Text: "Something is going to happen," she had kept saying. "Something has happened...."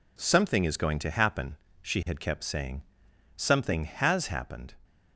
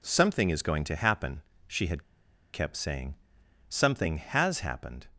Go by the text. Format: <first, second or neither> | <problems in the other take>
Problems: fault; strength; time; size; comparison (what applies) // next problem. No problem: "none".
first | pauses between "had" and "kept"; noticeable; at 2.0 s; 0.50 s long